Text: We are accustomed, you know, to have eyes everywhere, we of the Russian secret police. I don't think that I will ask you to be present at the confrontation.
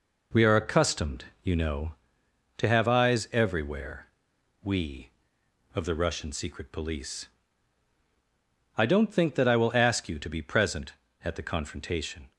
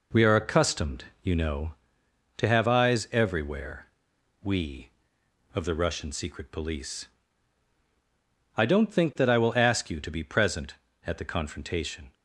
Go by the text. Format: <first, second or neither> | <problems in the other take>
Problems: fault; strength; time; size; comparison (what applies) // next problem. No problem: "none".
neither | none